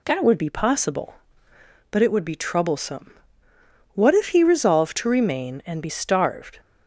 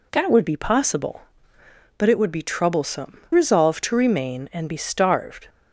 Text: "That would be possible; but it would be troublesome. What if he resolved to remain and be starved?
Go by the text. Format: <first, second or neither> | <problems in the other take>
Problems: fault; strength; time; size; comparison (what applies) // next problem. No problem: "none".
first | skips "What if he"; at 3.2 s